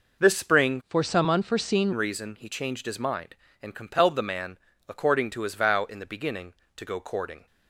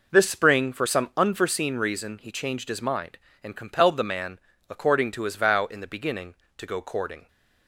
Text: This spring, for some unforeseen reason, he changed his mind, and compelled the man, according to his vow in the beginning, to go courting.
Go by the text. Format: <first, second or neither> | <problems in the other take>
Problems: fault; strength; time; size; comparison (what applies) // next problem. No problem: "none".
second | changes voice from "for" to "unforeseen"; from 0.8 to 1.9 s; 1.1 s long